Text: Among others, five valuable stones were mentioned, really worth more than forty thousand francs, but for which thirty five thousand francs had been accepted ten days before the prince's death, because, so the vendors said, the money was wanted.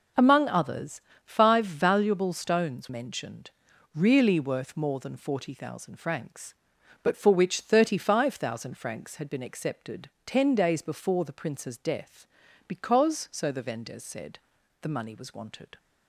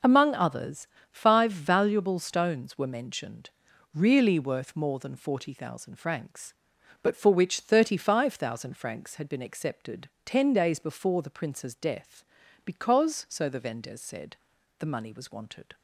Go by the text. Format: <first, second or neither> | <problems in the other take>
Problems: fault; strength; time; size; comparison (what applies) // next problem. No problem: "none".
second | skips "were"; at 2.8 s // pauses between "accepted" and "ten"; slight; at 10.0 s; 0.16 s long; slight in the second